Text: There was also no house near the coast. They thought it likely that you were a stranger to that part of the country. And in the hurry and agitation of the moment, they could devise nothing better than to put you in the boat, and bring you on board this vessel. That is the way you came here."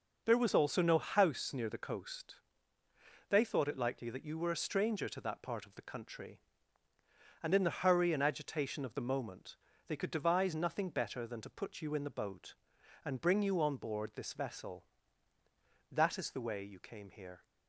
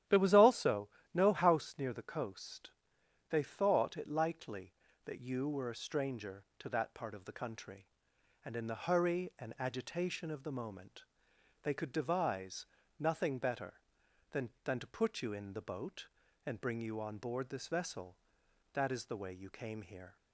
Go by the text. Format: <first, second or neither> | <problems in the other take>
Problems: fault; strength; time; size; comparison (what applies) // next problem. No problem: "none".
first | starts louder than the rest; strong; until 1.3 s; 11.5 dB // pauses between "also" and "no"; slight; at 0.8 s; 0.26 s long // pauses between "devise" and "nothing"; slight; at 12.6 s; 0.32 s long // says "than" twice; at 14.6 s